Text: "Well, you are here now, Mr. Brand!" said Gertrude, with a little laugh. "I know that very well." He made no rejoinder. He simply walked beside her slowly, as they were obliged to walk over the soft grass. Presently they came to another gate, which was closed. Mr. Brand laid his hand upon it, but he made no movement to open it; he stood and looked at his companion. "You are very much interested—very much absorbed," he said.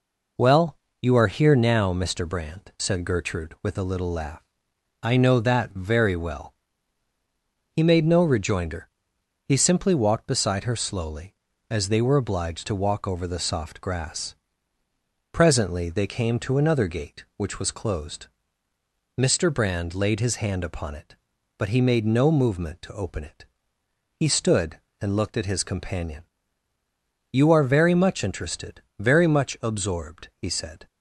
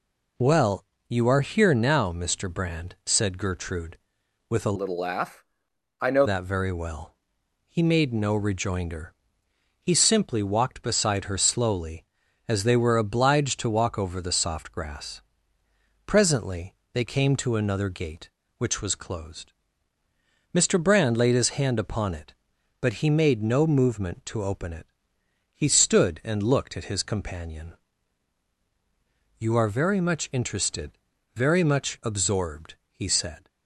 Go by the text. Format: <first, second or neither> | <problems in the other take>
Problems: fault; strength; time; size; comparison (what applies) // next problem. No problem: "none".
first | changes voice from "little" to "know"; from 4.7 to 6.2 s; 1.5 s long // pauses between "Presently" and "they"; slight; at 16.7 s; 0.18 s long